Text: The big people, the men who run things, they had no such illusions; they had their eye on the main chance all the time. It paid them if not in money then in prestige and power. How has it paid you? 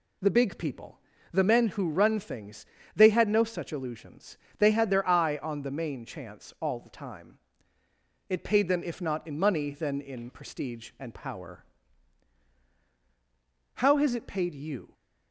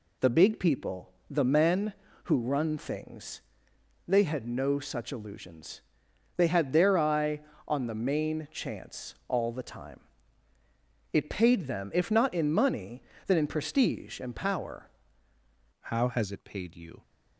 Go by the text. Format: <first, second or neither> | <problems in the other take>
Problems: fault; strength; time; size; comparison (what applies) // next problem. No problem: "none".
first | pauses between "chance" and "all"; slight; at 9.1 s; 0.16 s long // pauses between "money" and "then"; slight; at 13.0 s; 0.26 s long // changes voice at "How"; from 15.7 s on; 1.3 s long